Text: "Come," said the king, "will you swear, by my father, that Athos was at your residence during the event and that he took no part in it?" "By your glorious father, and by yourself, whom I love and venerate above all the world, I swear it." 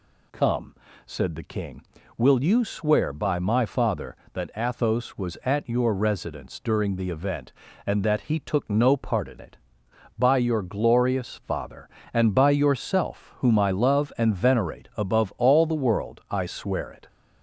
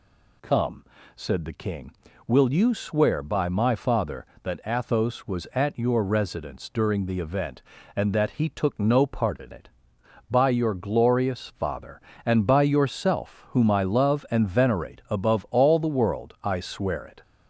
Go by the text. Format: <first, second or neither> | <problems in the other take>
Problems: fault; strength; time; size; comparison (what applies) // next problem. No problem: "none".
neither | none